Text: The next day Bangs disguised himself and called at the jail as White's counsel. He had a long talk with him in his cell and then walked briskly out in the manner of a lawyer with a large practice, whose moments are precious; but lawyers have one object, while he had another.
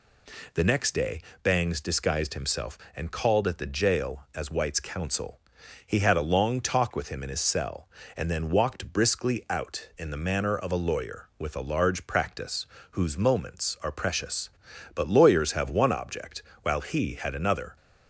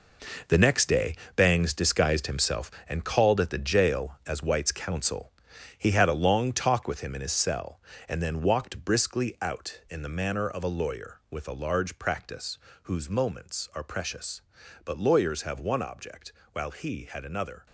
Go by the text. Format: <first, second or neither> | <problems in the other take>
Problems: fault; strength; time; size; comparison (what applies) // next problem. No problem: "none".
first | gets quieter; strong; throughout; 10 dB // pauses between "day" and "Bangs"; slight; at 1.1 s; 0.21 s long; slight in the first